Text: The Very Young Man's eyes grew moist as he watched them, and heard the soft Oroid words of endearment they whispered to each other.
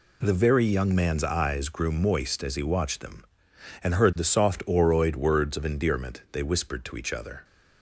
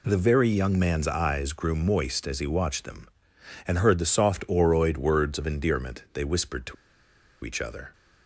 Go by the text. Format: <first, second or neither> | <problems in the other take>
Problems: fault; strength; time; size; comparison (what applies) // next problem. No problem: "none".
first | pauses between "to" and "each"; noticeable; at 6.7 s; 0.69 s long